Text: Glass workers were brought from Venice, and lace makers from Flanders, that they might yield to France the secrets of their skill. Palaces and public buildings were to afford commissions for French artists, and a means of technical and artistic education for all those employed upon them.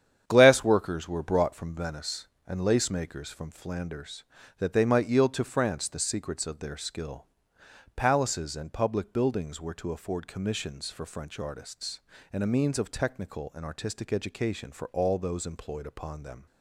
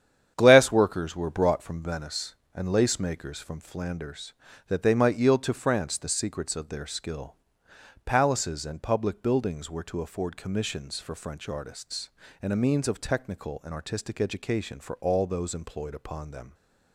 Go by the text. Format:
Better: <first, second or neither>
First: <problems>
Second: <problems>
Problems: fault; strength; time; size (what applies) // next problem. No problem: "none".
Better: neither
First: starts louder than the rest; strong; until 1.2 s; 9 dB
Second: starts louder than the rest; strong; until 1.3 s; 9 dB